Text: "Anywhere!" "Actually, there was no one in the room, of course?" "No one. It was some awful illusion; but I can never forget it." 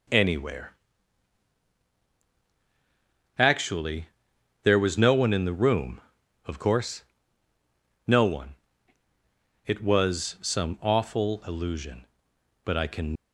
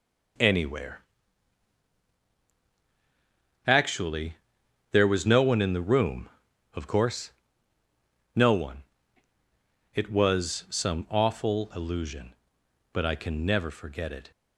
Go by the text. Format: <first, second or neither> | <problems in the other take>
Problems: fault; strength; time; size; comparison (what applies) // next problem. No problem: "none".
second | stops before "never forget it"; at 13.1 s